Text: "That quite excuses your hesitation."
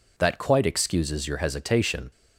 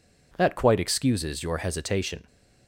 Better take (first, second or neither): neither